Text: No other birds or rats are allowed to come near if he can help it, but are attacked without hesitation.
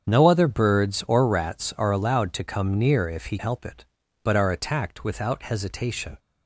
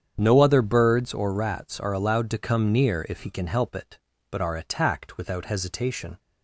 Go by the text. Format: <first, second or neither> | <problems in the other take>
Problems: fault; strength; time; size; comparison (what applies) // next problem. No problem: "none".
second | starts louder than the rest; strong; until 1.1 s; 7.5 dB; strong in the second // skips "can"; at 3.3 s